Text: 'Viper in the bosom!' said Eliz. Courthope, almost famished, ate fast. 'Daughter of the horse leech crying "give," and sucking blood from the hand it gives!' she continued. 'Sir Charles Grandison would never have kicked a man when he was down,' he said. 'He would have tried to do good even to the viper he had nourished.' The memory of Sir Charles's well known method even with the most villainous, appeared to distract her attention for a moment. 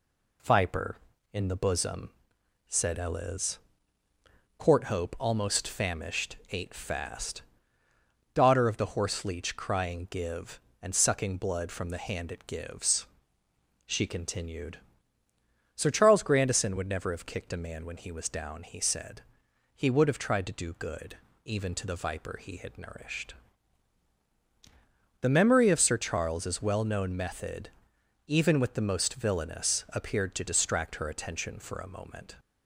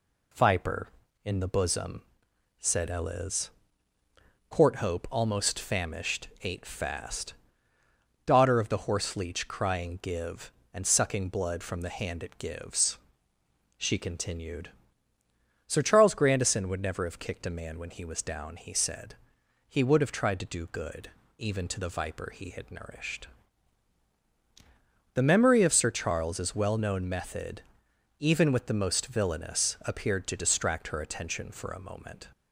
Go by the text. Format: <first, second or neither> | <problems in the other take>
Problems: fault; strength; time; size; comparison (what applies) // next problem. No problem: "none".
neither | pauses between "good" and "even"; slight; the same in both // pauses between "method" and "even"; noticeable; the same in both